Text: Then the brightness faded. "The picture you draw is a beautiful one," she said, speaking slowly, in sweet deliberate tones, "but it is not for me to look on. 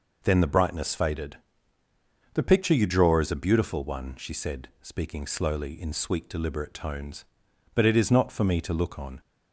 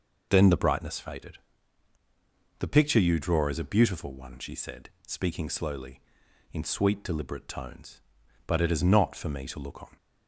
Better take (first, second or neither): neither